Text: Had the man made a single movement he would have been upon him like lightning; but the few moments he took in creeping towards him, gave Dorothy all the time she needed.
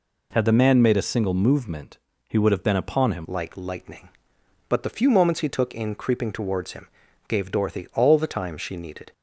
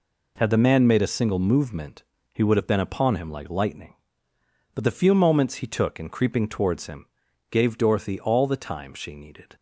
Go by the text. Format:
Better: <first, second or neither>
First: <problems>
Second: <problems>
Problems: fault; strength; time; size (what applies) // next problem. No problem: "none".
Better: second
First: pauses between "movement" and "he"; slight; at 1.9 s; 0.32 s long // changes voice at "like"; from 3.2 s on; 5.9 s long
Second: pauses between "movement" and "he"; slight; at 2.0 s; 0.32 s long